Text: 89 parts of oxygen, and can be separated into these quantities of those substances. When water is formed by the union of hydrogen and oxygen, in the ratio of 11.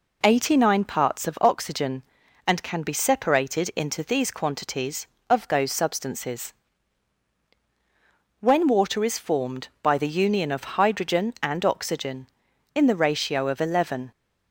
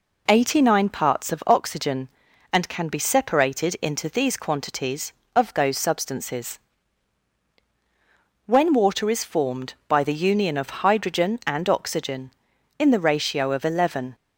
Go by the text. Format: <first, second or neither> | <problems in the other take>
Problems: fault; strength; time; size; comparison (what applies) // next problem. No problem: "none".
neither | none